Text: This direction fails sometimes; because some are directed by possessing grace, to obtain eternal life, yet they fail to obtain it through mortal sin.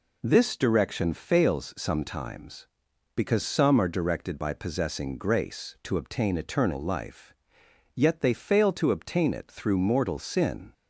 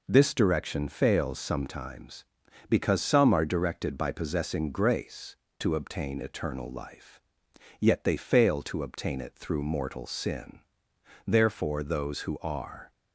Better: first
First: none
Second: goes on to say "Therefore those who are"; from 11.2 s on; 1.6 s long

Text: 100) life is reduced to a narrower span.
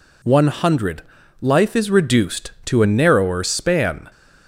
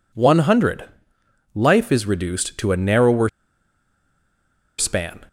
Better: first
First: none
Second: pauses between "narrower" and "span"; strong; at 3.2 s; 1.4 s long

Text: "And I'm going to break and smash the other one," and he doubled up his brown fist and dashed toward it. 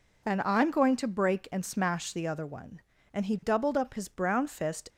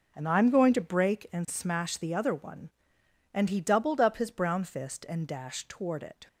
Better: second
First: stops before "and dashed toward it"; at 4.8 s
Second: none

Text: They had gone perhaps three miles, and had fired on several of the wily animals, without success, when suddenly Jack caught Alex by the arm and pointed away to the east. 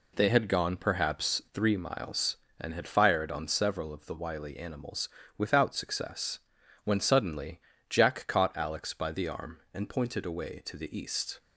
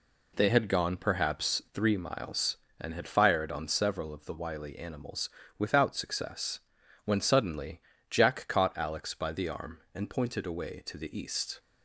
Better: neither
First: pauses between "suddenly" and "Jack"; slight; at 7.6 s; 0.28 s long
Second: pauses between "suddenly" and "Jack"; slight; at 7.8 s; 0.28 s long

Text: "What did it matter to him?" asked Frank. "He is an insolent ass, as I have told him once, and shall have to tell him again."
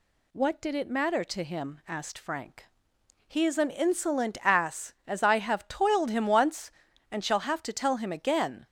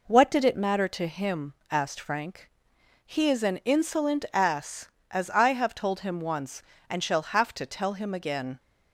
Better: second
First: says "toiled" for "told"; at 5.6 s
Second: none

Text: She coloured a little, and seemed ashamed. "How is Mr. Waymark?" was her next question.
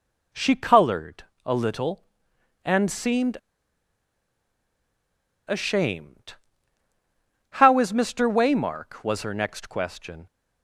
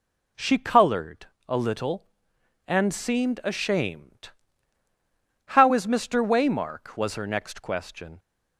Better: second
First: pauses between "coloured" and "a"; slight; at 1.2 s; 0.20 s long // pauses between "seemed" and "ashamed"; strong; at 3.3 s; 2.0 s long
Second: pauses between "coloured" and "a"; slight; at 1.2 s; 0.20 s long

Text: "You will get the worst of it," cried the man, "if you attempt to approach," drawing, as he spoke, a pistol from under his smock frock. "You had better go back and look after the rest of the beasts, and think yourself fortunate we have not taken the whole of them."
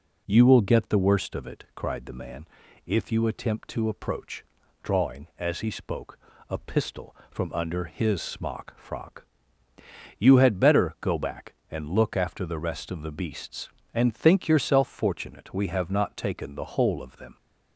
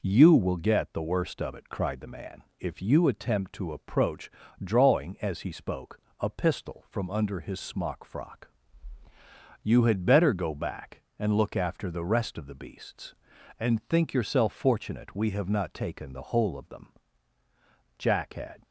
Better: first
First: none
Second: goes on to say "Jack had"; noticeable; from 17.9 s on; 0.64 s long

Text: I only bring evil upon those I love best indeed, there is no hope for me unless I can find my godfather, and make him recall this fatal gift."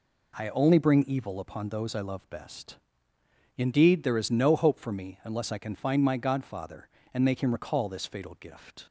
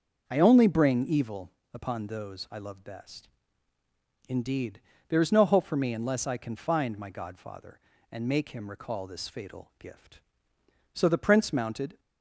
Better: first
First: pauses between "best" and "indeed"; noticeable; at 2.7 s; 0.78 s long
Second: starts louder than the rest; noticeable; until 1.2 s; 6 dB // pauses between "evil" and "upon"; slight; at 1.5 s; 0.20 s long // pauses between "best" and "indeed"; at 3.2 s; 1.0 s long // goes on to say "So the prince mounted"; noticeable; from 10.9 s on; 1.0 s long

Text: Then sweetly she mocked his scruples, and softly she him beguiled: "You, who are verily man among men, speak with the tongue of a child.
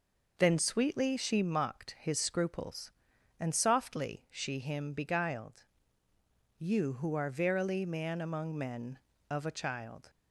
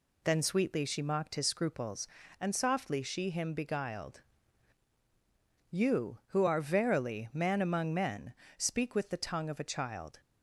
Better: second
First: skips "speak with the tongue"; at 9.1 s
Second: none

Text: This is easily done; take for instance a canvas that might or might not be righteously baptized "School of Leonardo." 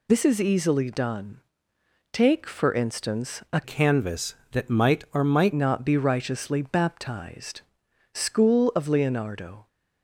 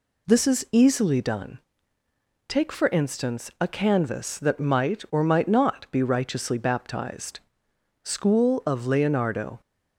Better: second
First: changes voice from "canvas" to "might"; from 3.6 to 5.5 s; 1.9 s long // pauses between "baptized" and "School"; noticeable; at 7.6 s; 0.54 s long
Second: pauses between "baptized" and "School"; noticeable; at 7.3 s; 0.64 s long

